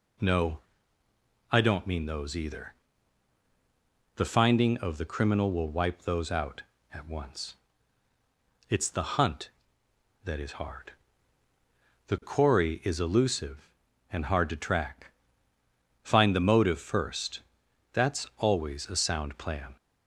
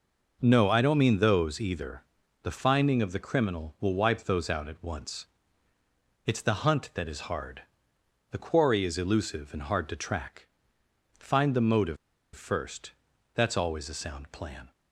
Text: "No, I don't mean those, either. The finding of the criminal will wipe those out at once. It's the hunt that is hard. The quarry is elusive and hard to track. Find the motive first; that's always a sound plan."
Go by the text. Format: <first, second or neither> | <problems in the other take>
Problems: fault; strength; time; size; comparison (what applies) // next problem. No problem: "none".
first | pauses between "motive" and "first"; at 11.9 s; 0.38 s long